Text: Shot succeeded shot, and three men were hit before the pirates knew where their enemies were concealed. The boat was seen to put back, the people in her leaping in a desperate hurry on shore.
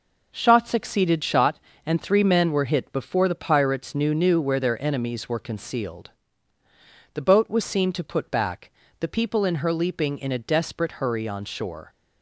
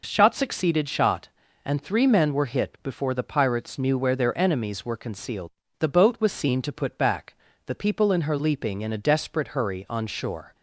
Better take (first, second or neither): second